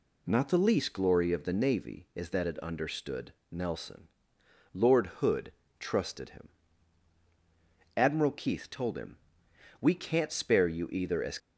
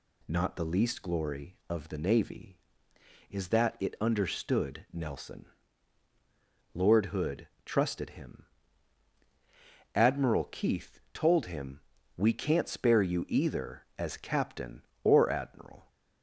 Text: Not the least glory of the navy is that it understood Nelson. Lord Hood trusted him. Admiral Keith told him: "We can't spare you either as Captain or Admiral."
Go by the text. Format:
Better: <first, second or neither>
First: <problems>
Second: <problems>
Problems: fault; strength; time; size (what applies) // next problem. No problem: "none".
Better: second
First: pauses between "understood" and "Nelson"; slight; at 3.3 s; 0.20 s long // pauses between "Hood" and "trusted"; slight; at 5.5 s; 0.28 s long // stops before "Captain or Admiral"; at 11.3 s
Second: pauses between "Hood" and "trusted"; slight; at 7.4 s; 0.16 s long